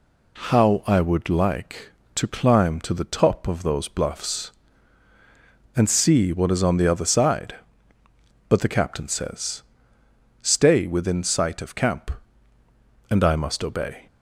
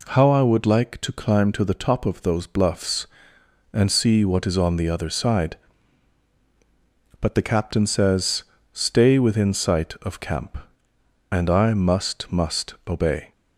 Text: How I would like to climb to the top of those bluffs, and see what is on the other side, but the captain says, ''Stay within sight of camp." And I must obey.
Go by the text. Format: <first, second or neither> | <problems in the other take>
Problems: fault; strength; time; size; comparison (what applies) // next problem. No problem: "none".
first | says "must" twice; at 12.3 s